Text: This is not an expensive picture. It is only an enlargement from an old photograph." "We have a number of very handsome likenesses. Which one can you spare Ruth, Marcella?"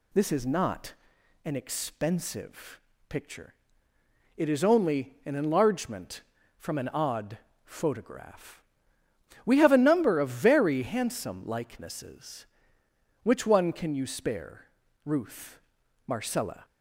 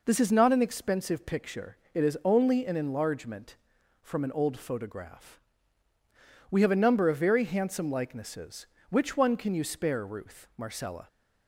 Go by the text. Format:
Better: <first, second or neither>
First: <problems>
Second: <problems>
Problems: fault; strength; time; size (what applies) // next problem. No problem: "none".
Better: second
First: pauses between "not" and "an"; noticeable; at 0.9 s; 0.52 s long // pauses between "expensive" and "picture"; slight; at 2.8 s; 0.28 s long // says "odd" for "old"; at 6.8 s // pauses between "spare" and "Ruth"; at 14.6 s; 0.38 s long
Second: none